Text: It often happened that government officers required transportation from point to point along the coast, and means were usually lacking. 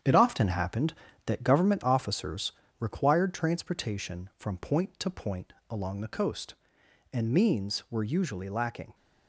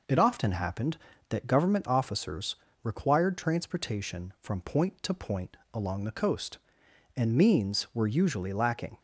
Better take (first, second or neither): second